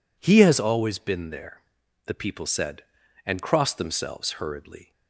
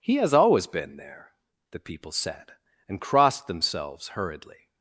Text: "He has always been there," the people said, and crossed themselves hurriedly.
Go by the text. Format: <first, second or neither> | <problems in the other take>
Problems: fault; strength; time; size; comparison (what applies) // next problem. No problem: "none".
neither | none